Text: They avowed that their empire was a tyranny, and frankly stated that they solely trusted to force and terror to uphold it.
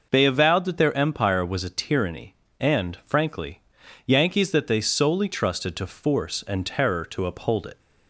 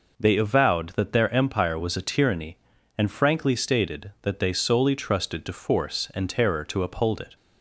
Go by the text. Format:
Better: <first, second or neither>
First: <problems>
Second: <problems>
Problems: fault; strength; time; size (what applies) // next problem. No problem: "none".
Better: second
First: says "yankees" for "stated"; at 4.0 s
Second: none